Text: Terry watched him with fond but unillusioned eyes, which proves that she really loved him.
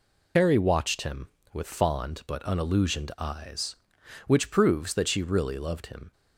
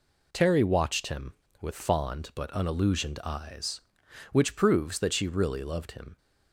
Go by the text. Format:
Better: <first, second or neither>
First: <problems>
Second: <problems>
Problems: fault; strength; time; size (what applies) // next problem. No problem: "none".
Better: second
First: loses the start of "Terry"; at 0.3 s; 80 ms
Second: none